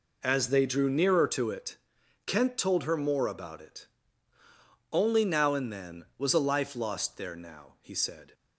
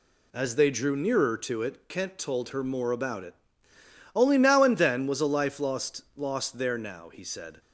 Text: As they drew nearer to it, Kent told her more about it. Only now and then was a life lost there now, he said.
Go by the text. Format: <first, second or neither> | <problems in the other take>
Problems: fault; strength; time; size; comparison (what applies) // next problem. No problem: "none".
first | says "lost" twice; at 6.1 s